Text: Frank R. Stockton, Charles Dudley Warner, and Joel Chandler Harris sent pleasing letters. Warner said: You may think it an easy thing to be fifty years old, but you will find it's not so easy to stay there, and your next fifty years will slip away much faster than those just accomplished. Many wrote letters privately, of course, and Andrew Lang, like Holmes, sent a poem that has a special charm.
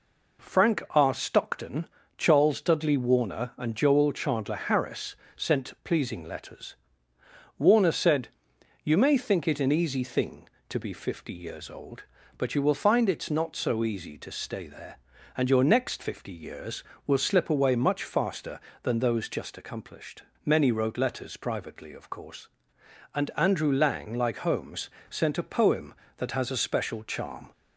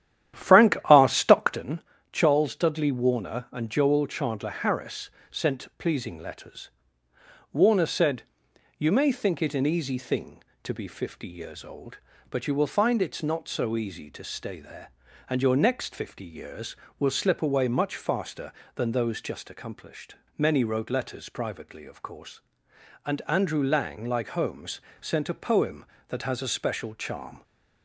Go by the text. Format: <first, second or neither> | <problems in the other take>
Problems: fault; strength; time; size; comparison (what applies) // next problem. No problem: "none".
first | starts louder than the rest; strong; until 1.7 s; 11 dB // pauses between "Harris" and "sent"; slight; at 5.0 s; 0.22 s long; slight in the first